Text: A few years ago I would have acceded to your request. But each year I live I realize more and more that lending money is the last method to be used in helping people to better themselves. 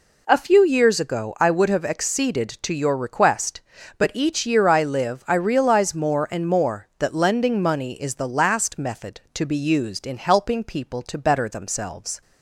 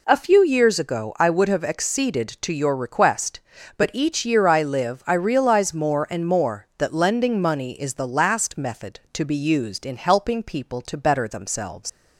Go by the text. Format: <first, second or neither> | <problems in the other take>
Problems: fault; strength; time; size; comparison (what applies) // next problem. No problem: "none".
first | leaves "themselves" unfinished; at 11.8 s; 100 ms